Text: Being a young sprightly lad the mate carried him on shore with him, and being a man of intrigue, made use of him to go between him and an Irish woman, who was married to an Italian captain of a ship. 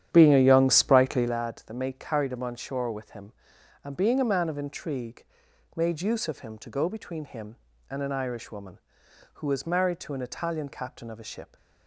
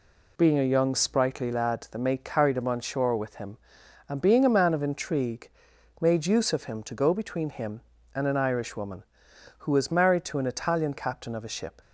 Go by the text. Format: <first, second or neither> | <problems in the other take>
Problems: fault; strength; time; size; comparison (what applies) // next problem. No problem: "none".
second | starts louder than the rest; strong; until 1.4 s; 10 dB